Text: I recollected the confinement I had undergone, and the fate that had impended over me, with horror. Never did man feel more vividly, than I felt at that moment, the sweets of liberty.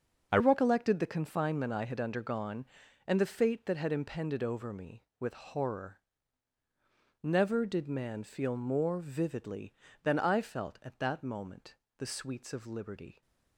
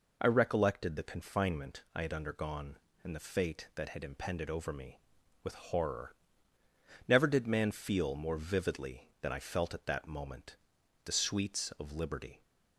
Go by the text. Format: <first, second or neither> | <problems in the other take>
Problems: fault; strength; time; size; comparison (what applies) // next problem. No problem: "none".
second | changes voice at "recollected"; from 0.3 s on; 12.9 s long